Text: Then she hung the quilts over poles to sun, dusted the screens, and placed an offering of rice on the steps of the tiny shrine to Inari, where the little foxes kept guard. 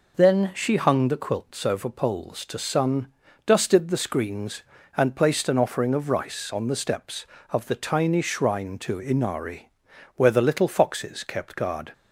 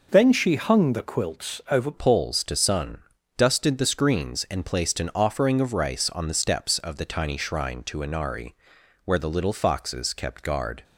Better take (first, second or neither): first